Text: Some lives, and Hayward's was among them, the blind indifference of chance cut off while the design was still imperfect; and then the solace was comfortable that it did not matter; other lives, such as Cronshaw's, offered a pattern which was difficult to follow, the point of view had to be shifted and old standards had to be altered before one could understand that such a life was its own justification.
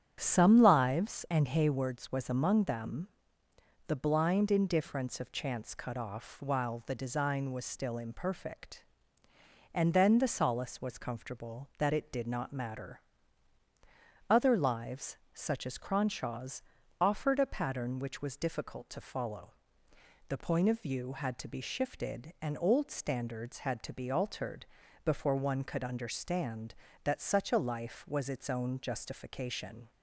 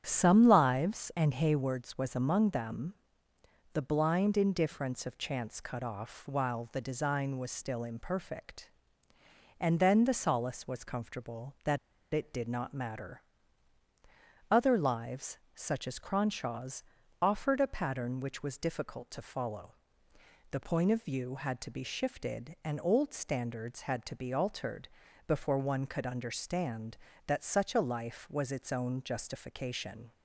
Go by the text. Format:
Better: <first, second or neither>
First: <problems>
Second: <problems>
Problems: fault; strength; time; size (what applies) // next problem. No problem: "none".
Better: first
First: starts louder than the rest; strong; until 1.2 s; 8.5 dB // pauses between "altered" and "before"; at 24.6 s; 0.40 s long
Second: starts louder than the rest; strong; until 1.0 s; 8.5 dB // pauses between "that" and "it"; at 11.7 s; 0.36 s long // pauses between "altered" and "before"; at 24.8 s; 0.40 s long